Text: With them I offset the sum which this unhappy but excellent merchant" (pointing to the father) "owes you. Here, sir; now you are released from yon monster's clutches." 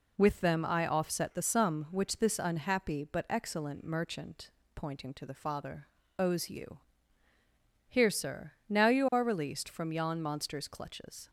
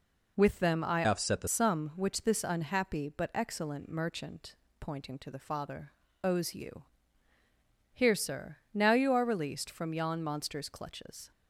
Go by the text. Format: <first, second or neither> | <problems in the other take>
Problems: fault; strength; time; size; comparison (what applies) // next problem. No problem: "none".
first | changes voice from "offset" to "the"; from 1.0 to 1.4 s; 0.4 s long